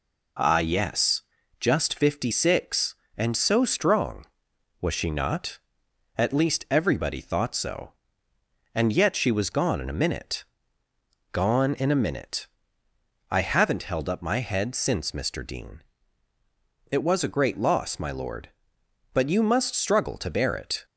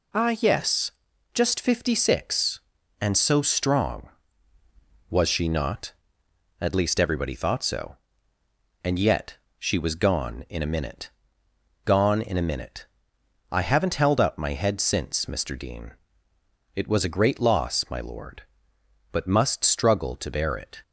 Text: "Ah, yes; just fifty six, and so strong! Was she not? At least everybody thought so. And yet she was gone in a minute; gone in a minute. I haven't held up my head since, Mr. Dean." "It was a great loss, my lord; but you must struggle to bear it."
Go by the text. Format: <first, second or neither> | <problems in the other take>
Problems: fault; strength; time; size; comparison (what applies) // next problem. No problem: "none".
first | pauses between "yet" and "she"; slight; at 9.3 s; 0.22 s long // skips "you"; at 19.2 s